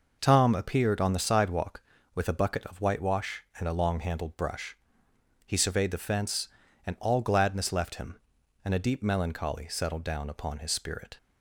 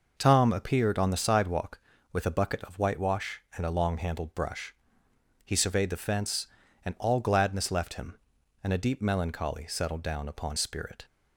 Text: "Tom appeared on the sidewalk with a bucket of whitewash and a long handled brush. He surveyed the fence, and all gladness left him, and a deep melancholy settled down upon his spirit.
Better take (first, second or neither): first